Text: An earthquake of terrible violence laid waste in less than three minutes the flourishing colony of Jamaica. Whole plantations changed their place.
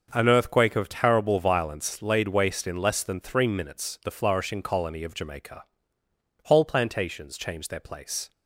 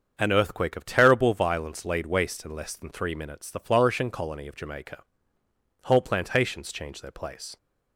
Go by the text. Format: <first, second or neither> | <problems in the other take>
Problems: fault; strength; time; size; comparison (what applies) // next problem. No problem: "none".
neither | starts louder than the rest; the same in both